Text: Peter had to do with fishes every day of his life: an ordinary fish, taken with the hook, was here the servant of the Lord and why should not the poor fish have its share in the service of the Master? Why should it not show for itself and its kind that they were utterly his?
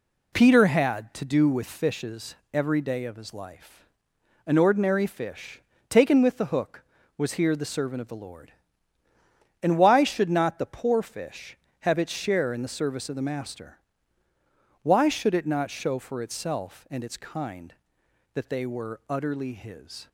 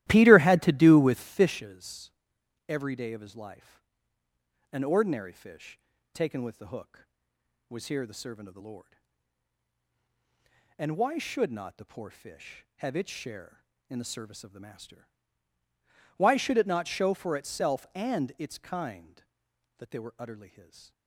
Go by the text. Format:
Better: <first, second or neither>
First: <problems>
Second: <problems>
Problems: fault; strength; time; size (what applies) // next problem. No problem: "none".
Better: first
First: pauses between "fishes" and "every"; slight; at 2.3 s; 0.18 s long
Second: starts louder than the rest; strong; until 1.6 s; 15 dB // pauses between "fishes" and "every"; noticeable; at 2.1 s; 0.56 s long